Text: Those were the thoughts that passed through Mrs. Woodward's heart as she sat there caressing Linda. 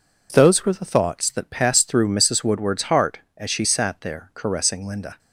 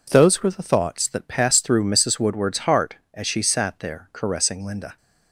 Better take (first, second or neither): neither